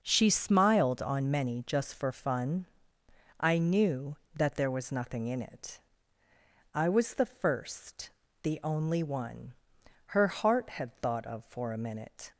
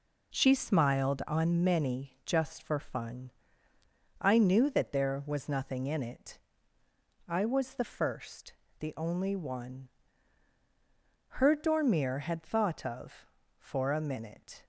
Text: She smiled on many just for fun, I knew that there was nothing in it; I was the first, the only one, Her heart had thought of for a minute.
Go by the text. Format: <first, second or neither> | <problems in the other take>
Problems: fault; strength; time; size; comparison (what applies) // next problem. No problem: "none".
first | says "dormir" for "heart"; at 11.5 s